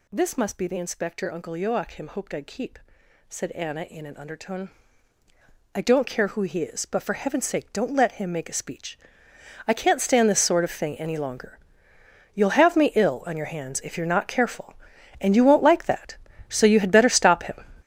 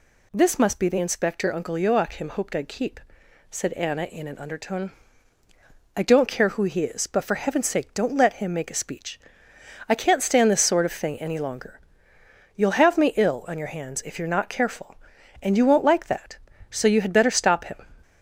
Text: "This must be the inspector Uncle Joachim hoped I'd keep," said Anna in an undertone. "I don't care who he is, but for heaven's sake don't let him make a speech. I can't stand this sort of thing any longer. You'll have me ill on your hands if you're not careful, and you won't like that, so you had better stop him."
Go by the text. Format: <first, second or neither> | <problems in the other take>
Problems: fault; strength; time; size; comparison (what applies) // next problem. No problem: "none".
second | gets louder; strong; throughout; 10.5 dB